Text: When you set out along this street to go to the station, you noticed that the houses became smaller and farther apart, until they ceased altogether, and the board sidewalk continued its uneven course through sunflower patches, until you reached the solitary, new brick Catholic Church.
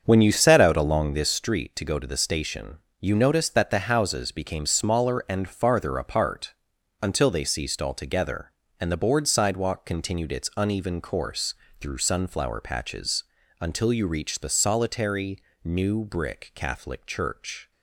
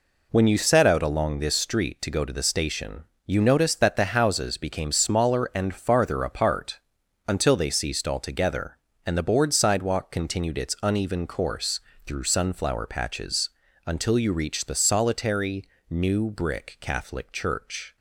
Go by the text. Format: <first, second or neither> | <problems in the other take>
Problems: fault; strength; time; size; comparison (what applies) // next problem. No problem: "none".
second | starts louder than the rest; until 1.4 s; 7 dB // pauses between "course" and "through"; slight; at 11.5 s; 0.26 s long; slight in the second